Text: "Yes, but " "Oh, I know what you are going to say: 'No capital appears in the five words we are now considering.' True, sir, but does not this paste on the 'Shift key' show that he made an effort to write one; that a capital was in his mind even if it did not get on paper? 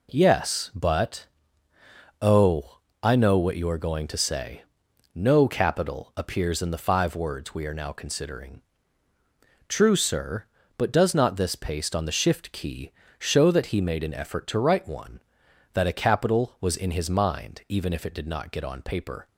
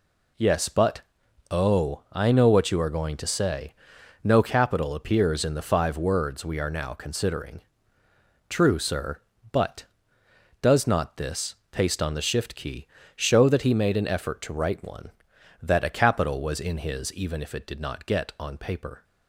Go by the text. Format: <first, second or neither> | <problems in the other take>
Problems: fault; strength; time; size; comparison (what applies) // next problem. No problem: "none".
first | pauses between "this" and "paste"; slight; at 11.5 s; 0.16 s long // pauses between "key" and "show"; slight; at 12.8 s; 0.26 s long; slight in the first // skips "mind"; at 17.1 s